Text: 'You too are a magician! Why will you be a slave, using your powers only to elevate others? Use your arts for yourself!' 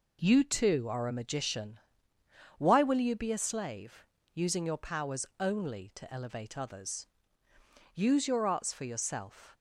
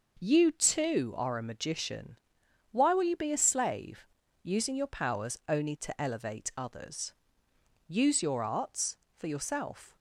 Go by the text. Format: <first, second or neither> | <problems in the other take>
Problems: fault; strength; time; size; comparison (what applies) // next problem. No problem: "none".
neither | none